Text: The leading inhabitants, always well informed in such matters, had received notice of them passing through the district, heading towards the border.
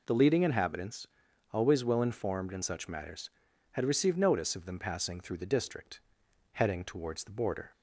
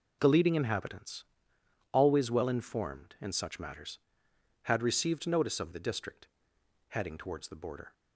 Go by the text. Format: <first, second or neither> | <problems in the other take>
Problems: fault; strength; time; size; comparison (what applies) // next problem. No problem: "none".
first | skips "them passing through"; at 5.7 s